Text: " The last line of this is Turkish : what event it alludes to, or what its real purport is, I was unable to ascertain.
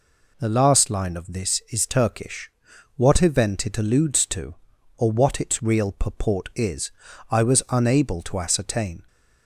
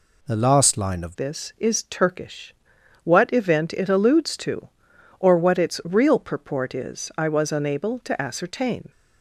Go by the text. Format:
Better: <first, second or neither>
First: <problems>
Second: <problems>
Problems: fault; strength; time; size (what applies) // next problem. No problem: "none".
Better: first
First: none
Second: changes voice at "this"; from 1.1 s on; 7.7 s long